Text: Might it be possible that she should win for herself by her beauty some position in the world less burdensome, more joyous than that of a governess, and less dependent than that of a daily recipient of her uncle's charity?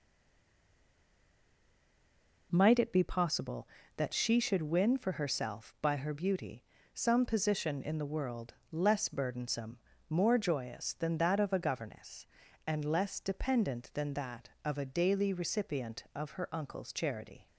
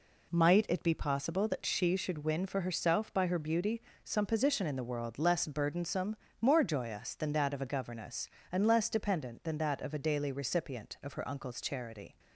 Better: second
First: stays silent before the first word; until 2.5 s; 2.5 s long // pauses between "beauty" and "some"; slight; at 6.6 s; 0.28 s long // pauses between "world" and "less"; slight; at 8.5 s; 0.18 s long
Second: pauses between "beauty" and "some"; slight; at 3.8 s; 0.24 s long

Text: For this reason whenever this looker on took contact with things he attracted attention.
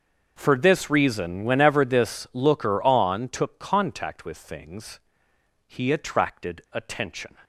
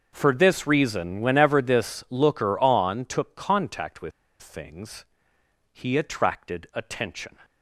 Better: first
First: starts louder than the rest; until 1.3 s; 6.5 dB // pauses between "things" and "he"; noticeable; at 4.9 s; 0.66 s long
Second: starts louder than the rest; until 1.1 s; 6 dB // pauses between "with" and "things"; slight; at 4.1 s; 0.31 s long // pauses between "things" and "he"; noticeable; at 5.0 s; 0.66 s long

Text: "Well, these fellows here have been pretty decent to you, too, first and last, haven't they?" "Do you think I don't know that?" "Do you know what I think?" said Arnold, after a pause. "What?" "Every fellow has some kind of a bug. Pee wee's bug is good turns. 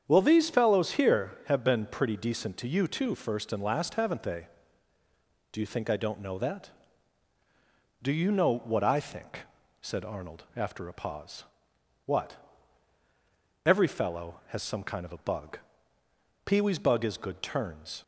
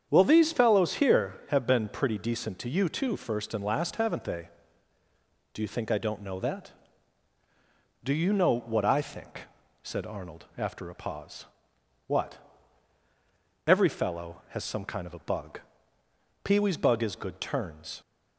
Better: neither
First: starts louder than the rest; strong; until 1.0 s; 8 dB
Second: starts louder than the rest; strong; until 1.1 s; 8 dB

